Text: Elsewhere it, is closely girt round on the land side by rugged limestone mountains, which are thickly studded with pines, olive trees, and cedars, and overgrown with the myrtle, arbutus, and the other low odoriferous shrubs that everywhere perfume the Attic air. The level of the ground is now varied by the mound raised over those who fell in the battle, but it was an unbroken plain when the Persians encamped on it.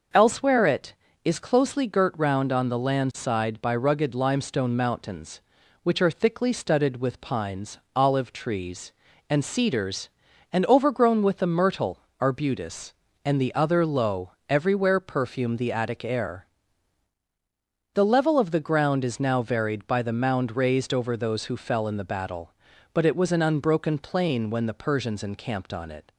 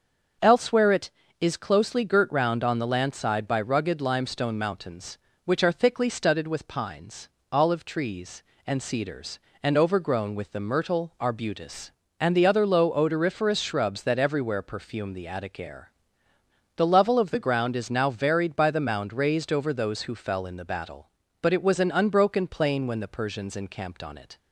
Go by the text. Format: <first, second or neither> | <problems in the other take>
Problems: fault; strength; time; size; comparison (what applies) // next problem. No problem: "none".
second | starts louder than the rest; noticeable; until 1.4 s; 6 dB; also in the second // skips "odoriferous shrubs that"; at 14.3 s